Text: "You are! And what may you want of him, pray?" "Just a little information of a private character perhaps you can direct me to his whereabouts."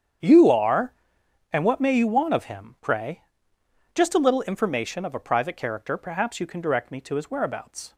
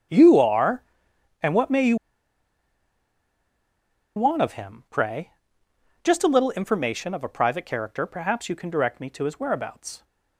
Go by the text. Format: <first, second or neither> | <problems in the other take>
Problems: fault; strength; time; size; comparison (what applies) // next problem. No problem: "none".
first | starts louder than the rest; strong; until 1.7 s; 8.5 dB; strong in the first // pauses between "you" and "want"; strong; at 1.9 s; 2.2 s long